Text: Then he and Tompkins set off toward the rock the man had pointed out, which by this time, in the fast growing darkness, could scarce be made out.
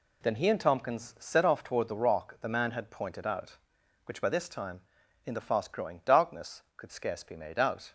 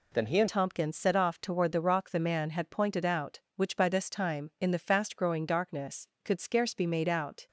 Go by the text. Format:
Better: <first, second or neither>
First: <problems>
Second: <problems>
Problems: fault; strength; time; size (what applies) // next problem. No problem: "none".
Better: first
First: none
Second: changes voice at "Tompkins"; from 0.4 s on; 7.0 s long